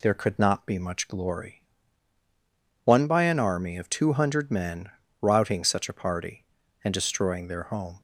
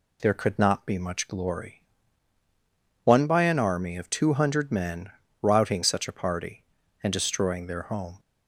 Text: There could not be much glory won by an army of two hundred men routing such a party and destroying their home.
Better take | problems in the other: neither | pauses between "glory" and "won"; the same in both // pauses between "men" and "routing"; slight; the same in both

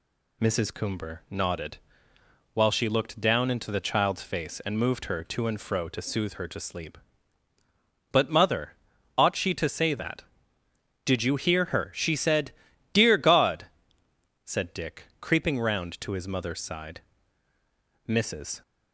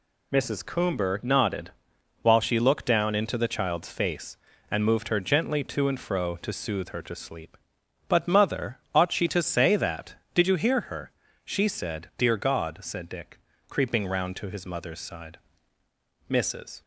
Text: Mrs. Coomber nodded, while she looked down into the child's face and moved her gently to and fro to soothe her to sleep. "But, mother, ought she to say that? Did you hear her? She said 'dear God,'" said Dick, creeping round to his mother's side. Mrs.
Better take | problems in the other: second | skips "gently"; at 5.2 s // pauses between "said" and "dear"; at 12.5 s; 0.40 s long

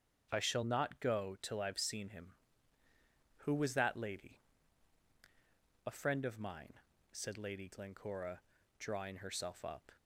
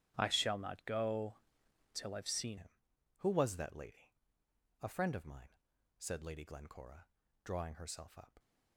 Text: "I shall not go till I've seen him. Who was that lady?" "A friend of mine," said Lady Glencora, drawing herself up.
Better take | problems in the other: first | starts louder than the rest; strong; until 1.1 s; 10 dB; also in the first // pauses between "go" and "till"; noticeable; at 1.3 s; 0.58 s long // changes voice at "him"; from 2.5 s on; 5.8 s long

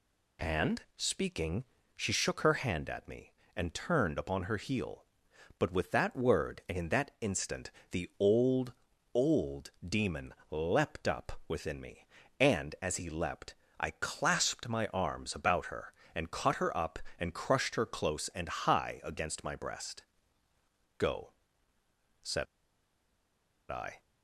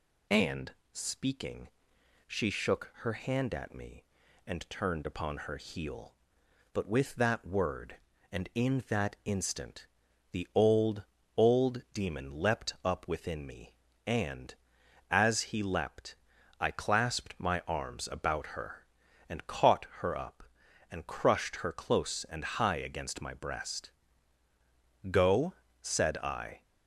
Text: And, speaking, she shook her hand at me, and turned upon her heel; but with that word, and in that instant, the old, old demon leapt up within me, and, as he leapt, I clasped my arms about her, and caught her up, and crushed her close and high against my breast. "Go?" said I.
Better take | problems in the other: second | pauses between "old" and "demon"; slight; at 9.7 s; 0.16 s long // pauses between "demon" and "leapt"; slight; at 10.3 s; 0.18 s long // pauses between "said" and "I"; strong; at 22.4 s; 1.2 s long

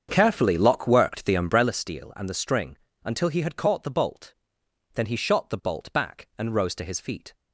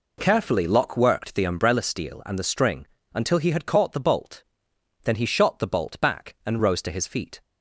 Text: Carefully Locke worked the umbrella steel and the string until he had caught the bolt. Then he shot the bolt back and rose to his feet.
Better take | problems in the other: second | starts louder than the rest; strong; until 1.8 s; 7 dB // pauses between "string" and "until"; slight; at 2.7 s; 0.28 s long; slight in the second

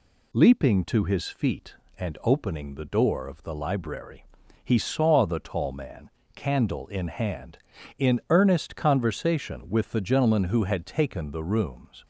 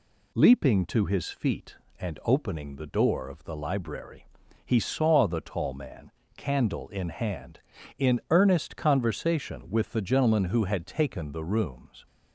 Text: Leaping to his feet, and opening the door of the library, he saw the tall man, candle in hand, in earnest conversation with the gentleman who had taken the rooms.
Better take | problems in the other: neither | none

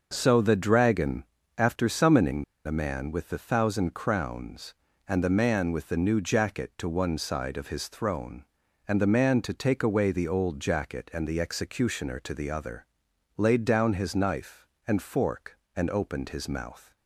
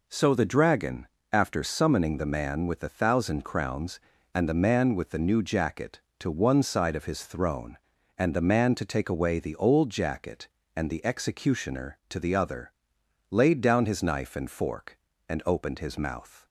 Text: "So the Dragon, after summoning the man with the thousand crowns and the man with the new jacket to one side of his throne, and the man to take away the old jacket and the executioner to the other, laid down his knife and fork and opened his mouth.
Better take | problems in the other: second | pauses between "summoning" and "the"; slight; at 2.4 s; 0.23 s long

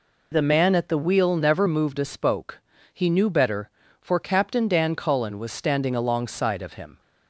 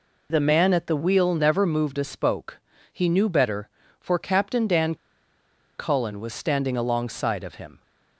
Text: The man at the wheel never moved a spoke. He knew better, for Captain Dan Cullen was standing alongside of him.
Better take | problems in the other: first | pauses between "Dan" and "Cullen"; noticeable; at 4.9 s; 0.83 s long

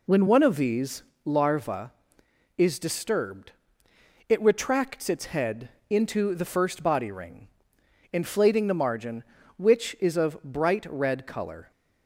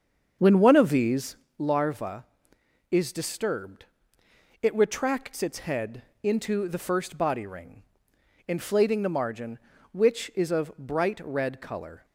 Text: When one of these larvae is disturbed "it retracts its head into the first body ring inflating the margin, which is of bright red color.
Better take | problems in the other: first | starts louder than the rest; until 1.3 s; 7 dB // pauses between "these" and "larvae"; slight; at 1.3 s; 0.22 s long; slight in the first // pauses between "disturbed" and "it"; noticeable; at 3.8 s; 0.78 s long; noticeable in the first // pauses between "head" and "into"; slight; at 6.0 s; 0.22 s long; slight in the first // pauses between "ring" and "inflating"; noticeable; at 7.8 s; 0.66 s long; noticeable in the first

